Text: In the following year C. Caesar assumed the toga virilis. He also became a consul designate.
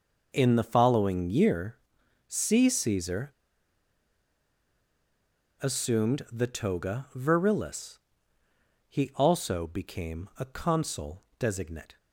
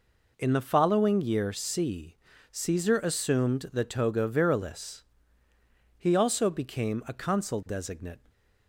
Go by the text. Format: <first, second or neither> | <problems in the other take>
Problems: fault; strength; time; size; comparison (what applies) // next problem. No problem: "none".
second | pauses between "year" and "C"; noticeable; at 1.7 s; 0.50 s long // pauses between "Caesar" and "assumed"; strong; at 3.3 s; 2.2 s long // pauses between "consul" and "designate"; slight; at 11.2 s; 0.18 s long